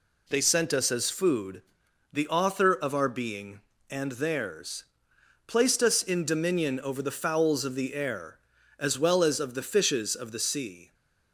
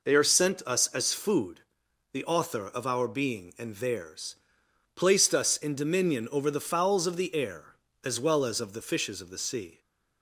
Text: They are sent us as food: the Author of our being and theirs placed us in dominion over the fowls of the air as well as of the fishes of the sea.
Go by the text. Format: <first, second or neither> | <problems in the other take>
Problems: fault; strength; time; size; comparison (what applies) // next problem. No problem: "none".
second | skips "are"; at 0.4 s // pauses between "theirs" and "placed"; noticeable; at 4.8 s; 0.64 s long; noticeable in the second